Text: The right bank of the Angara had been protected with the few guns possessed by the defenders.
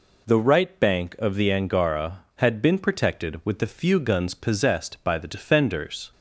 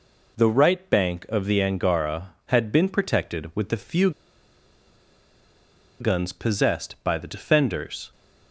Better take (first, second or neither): first